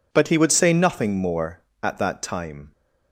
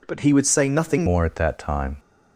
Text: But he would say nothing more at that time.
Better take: first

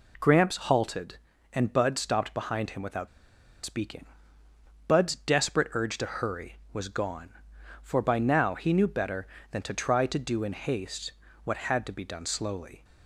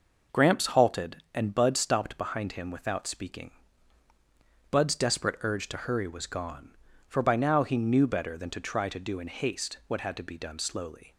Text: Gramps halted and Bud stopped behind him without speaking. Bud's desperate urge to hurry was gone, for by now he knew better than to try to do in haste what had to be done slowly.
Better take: second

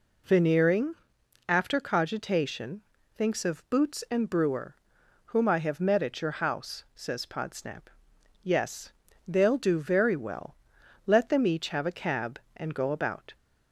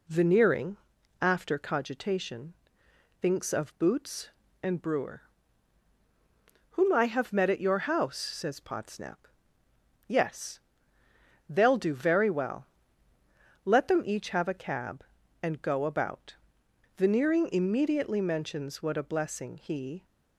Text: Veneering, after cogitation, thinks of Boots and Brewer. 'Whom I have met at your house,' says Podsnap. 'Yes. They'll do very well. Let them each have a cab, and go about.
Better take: first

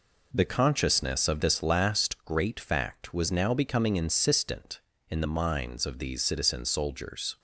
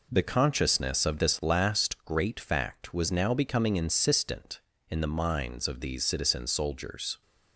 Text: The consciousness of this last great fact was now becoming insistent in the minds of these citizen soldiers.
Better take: neither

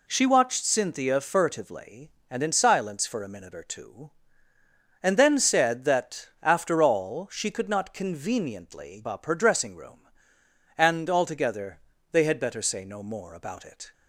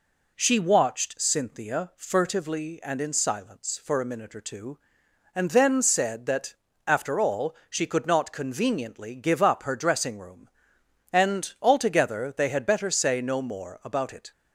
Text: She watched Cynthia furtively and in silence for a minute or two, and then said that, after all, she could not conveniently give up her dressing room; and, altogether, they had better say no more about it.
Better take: second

